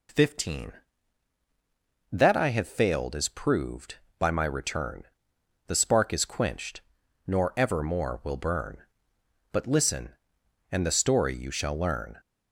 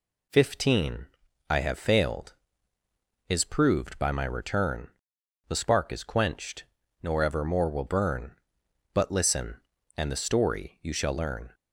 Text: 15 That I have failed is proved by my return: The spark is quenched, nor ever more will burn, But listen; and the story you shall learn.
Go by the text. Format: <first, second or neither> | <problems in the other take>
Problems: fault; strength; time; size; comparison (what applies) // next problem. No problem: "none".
first | skips "That"; at 1.2 s